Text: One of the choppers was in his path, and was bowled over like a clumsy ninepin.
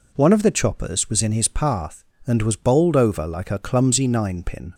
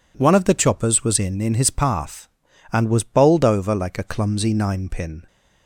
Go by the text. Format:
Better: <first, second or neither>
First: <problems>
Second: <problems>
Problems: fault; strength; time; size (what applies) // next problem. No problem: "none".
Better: first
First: none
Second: says "in" twice; at 1.4 s